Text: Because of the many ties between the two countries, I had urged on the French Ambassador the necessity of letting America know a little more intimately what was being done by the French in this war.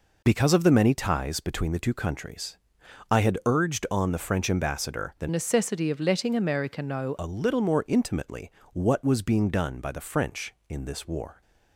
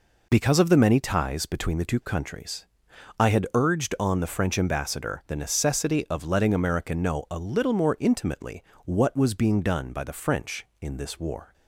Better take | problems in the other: second | changes voice from "necessity" to "know"; from 5.2 to 7.1 s; 1.9 s long // pauses between "intimately" and "what"; slight; at 8.5 s; 0.22 s long; slight in the second

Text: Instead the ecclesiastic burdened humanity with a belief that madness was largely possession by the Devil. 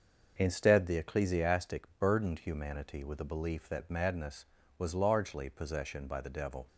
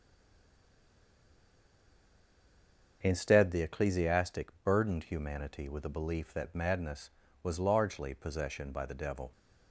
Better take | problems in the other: first | stays silent before the first word; strong; until 3.0 s; 3.0 s long // starts louder than the rest; until 4.0 s; 6.5 dB; also in the first

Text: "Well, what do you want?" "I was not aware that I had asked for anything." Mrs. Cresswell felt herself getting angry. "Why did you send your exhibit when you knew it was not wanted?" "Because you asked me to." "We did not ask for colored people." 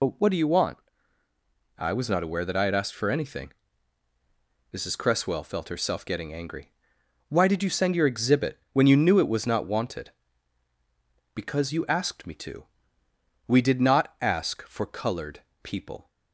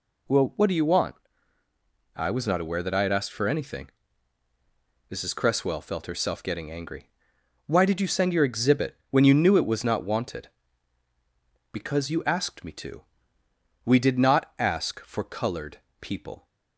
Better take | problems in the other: second | loses the start of "Well"; at 0.0 s; 120 ms // pauses between "colored" and "people"; slight; at 15.4 s; 0.22 s long; slight in the second

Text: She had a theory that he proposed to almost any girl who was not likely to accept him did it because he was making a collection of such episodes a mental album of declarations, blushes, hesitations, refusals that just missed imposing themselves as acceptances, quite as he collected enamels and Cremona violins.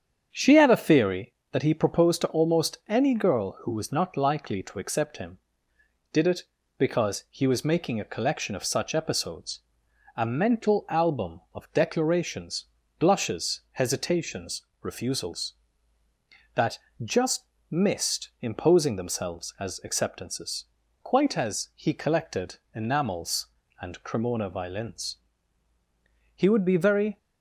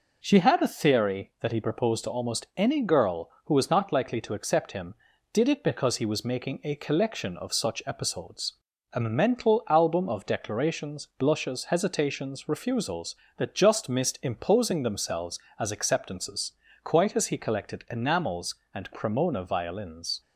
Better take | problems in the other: second | starts louder than the rest; strong; until 1.3 s; 8 dB // pauses between "episodes" and "a"; noticeable; at 9.5 s; 0.56 s long; also in the second // pauses between "that" and "just"; slight; at 16.7 s; 0.26 s long // pauses between "just" and "missed"; slight; at 17.4 s; 0.26 s long // pauses between "collected" and "enamels"; slight; at 22.5 s; 0.20 s long // goes on to say "He would be very"; noticeable; from 26.3 s on; 0.80 s long

